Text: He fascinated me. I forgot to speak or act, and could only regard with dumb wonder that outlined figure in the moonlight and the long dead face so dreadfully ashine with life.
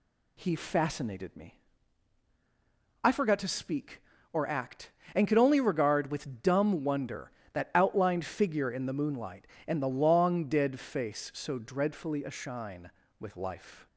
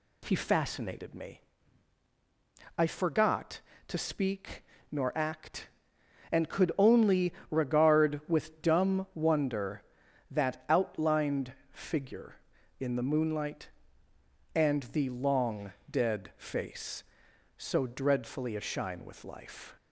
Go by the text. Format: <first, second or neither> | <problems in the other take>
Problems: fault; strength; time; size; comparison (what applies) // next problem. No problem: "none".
first | says "nor" for "or"; at 4.8 s // pauses between "only" and "regard"; slight; at 7.3 s; 0.18 s long // pauses between "outlined" and "figure"; slight; at 11.5 s; 0.18 s long // pauses between "long" and "dead"; slight; at 15.7 s; 0.18 s long